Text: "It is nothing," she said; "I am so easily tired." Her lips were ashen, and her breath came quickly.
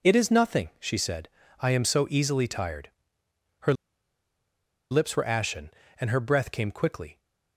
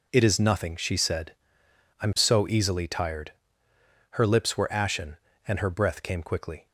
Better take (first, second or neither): second